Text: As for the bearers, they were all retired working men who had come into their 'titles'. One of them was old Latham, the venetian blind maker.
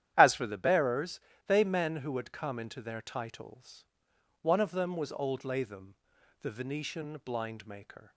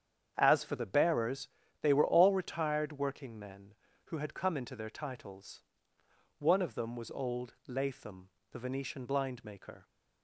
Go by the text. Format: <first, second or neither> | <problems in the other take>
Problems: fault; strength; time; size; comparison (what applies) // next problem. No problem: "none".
second | starts louder than the rest; strong; until 1.1 s; 11 dB; strong in the second // skips "were all retired working"; at 1.6 s